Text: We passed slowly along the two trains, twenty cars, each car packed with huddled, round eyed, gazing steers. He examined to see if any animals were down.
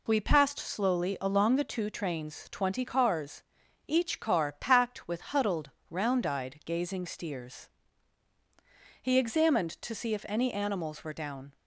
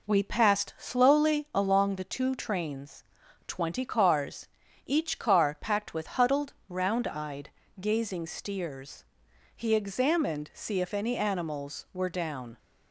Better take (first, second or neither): first